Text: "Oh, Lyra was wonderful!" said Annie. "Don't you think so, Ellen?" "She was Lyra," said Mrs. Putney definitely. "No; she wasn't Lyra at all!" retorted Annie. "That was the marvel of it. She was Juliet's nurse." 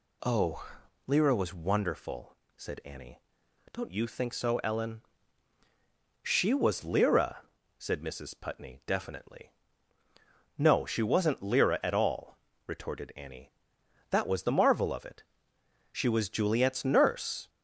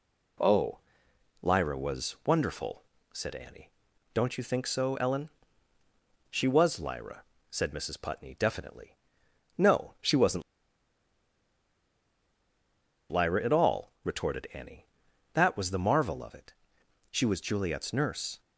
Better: first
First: none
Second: pauses between "wasn't" and "Lyra"; strong; at 10.4 s; 2.6 s long

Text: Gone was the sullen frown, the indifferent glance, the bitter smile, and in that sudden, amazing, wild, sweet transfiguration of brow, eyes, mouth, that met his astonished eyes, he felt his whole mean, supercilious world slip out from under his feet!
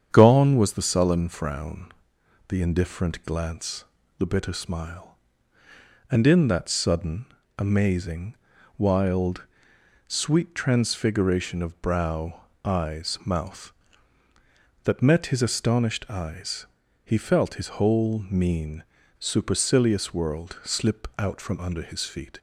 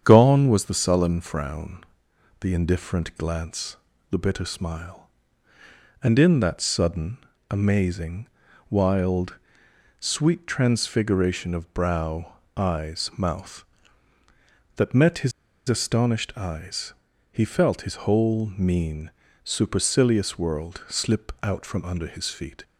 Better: first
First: starts louder than the rest; strong; until 1.1 s; 8 dB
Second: starts louder than the rest; strong; until 1.0 s; 8 dB // pauses between "his" and "astonished"; at 15.3 s; 0.37 s long

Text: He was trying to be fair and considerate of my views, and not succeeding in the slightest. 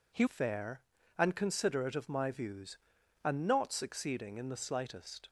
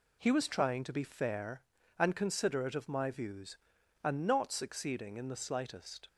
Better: second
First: skips "was trying to be"; at 0.2 s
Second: none

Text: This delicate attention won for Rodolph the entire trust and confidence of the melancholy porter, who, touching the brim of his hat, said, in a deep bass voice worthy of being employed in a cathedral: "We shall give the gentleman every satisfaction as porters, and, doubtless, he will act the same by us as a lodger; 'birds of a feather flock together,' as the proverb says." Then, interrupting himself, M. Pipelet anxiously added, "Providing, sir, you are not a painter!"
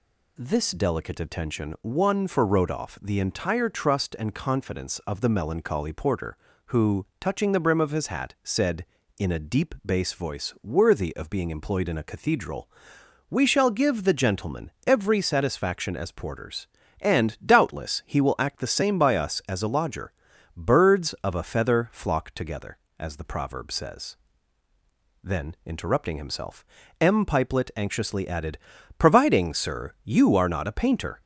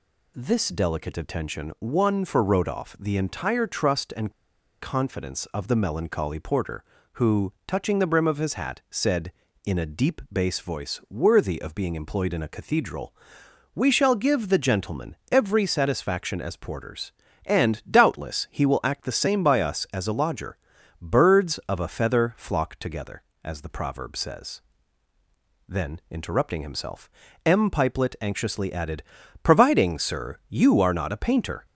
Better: first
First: pauses between "gentleman" and "every"; slight; at 14.6 s; 0.16 s long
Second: pauses between "and" and "confidence"; noticeable; at 4.3 s; 0.50 s long // pauses between "gentleman" and "every"; slight; at 15.1 s; 0.16 s long

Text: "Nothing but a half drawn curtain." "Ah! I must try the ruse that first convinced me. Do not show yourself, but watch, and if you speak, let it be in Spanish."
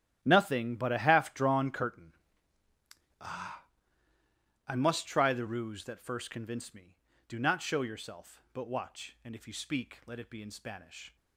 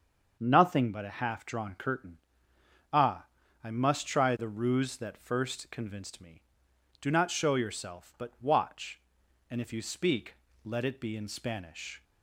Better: second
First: gets quieter; strong; throughout; 14.5 dB // starts louder than the rest; strong; until 1.2 s; 12.5 dB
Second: starts louder than the rest; until 1.4 s; 6.5 dB

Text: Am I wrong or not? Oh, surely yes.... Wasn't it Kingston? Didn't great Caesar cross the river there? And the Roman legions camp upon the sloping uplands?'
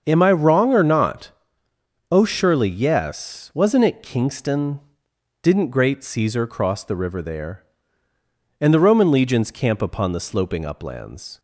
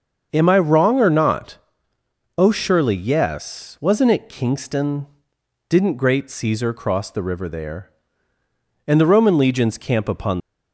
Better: first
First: starts louder than the rest; until 1.0 s; 7 dB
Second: starts louder than the rest; until 1.3 s; 6.5 dB // stops before "the sloping uplands"; at 10.3 s

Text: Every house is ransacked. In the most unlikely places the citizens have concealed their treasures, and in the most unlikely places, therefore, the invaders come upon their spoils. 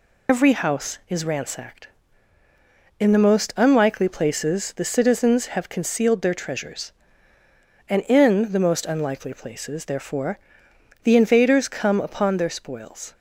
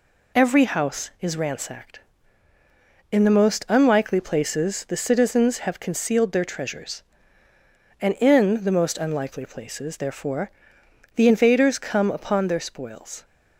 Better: second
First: loses the start of "Every"; at 0.2 s; 60 ms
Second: none

